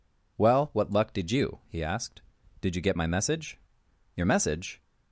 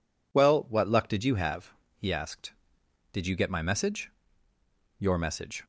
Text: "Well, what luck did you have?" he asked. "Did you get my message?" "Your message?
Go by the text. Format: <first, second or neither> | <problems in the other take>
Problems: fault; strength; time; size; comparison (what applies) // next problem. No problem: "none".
second | skips "have"; at 1.6 s